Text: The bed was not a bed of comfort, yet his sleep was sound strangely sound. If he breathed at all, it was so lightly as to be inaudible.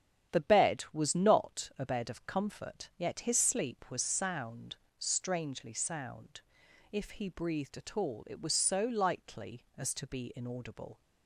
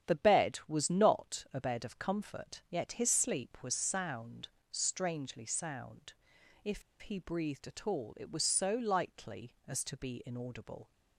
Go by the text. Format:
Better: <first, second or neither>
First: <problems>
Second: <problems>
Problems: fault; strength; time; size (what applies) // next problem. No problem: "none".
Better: first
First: starts louder than the rest; strong; until 1.4 s; 9.5 dB // pauses between "sound" and "strangely"; slight; at 4.7 s; 0.22 s long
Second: starts louder than the rest; strong; until 1.1 s; 9.5 dB // pauses between "sound" and "strangely"; slight; at 4.4 s; 0.22 s long // pauses between "If" and "he"; slight; at 6.8 s; 0.19 s long